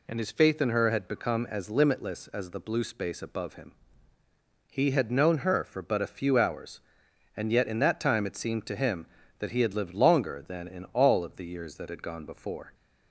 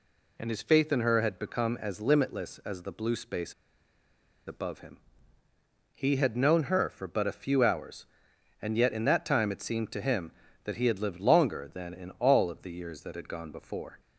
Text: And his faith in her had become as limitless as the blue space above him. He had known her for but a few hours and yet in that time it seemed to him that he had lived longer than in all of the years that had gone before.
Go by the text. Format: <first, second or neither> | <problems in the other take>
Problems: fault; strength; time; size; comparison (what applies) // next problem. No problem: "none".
first | pauses between "space" and "above"; noticeable; at 3.5 s; 0.94 s long